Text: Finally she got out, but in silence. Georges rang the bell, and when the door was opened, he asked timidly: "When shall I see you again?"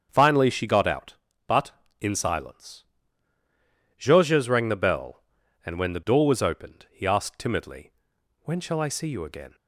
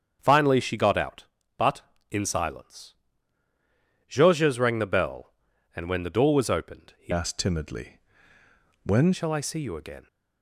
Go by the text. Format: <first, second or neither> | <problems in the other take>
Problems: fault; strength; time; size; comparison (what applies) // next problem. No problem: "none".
first | starts louder than the rest; strong; until 1.2 s; 7.5 dB; strong in the first // changes voice from "asked" to "When"; from 7.1 to 9.1 s; 2.0 s long